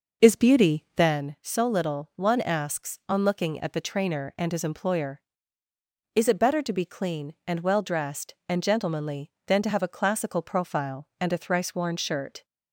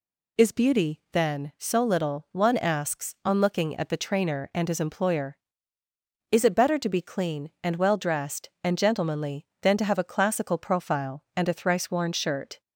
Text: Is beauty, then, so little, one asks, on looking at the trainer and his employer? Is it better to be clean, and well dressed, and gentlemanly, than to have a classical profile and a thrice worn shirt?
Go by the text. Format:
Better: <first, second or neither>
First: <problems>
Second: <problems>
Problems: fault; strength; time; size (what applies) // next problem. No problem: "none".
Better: second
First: starts louder than the rest; noticeable; until 1.3 s; 6 dB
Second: none